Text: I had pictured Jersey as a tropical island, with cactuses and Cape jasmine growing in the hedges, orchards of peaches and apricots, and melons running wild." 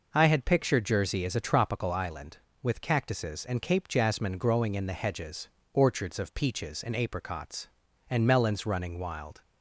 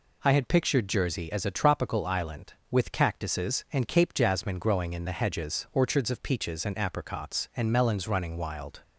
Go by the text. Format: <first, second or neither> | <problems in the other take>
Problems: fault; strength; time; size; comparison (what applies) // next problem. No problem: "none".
neither | none